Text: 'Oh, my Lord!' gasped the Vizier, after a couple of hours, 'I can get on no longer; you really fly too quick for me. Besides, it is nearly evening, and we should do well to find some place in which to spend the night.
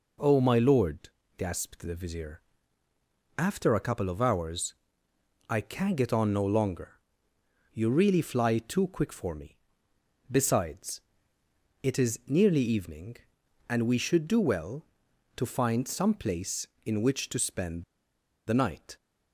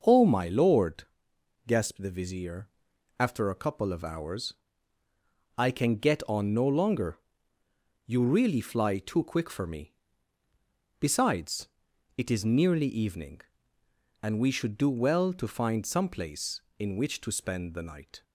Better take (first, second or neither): second